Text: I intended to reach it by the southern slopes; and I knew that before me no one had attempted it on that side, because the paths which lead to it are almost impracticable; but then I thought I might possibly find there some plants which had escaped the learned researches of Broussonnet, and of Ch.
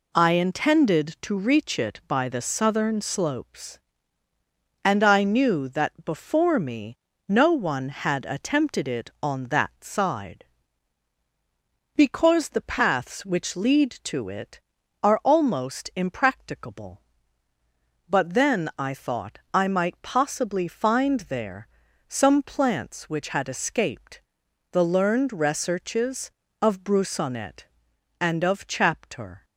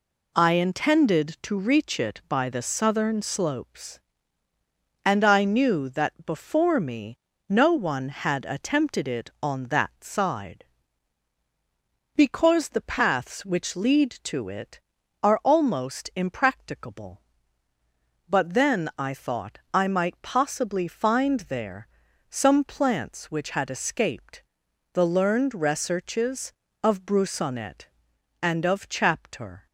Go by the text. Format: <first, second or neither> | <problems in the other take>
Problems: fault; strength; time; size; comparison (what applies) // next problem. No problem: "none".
neither | pauses between "me" and "no"; slight; the same in both // pauses between "thought" and "I"; slight; the same in both // pauses between "there" and "some"; the same in both // pauses between "escaped" and "the"; noticeable; the same in both